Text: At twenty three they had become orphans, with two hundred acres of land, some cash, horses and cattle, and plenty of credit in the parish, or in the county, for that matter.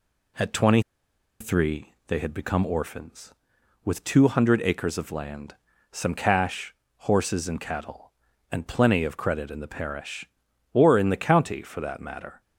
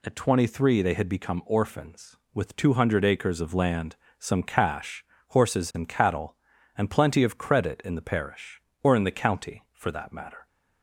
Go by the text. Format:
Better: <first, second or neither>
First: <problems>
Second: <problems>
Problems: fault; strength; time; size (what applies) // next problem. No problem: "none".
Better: second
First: pauses between "twenty" and "three"; noticeable; at 0.8 s; 0.59 s long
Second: none